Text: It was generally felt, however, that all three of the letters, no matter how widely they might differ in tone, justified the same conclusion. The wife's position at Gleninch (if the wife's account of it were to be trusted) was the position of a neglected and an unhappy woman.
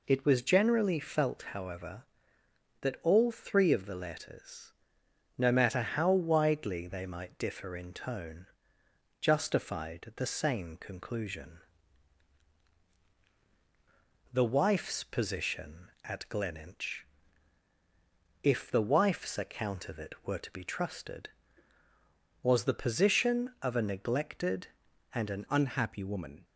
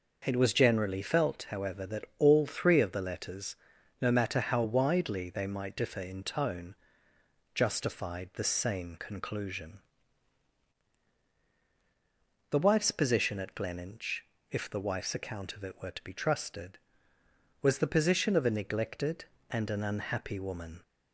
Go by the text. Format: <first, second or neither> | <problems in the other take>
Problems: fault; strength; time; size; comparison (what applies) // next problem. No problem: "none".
second | changes voice at "unhappy"; from 25.4 s on; 1.0 s long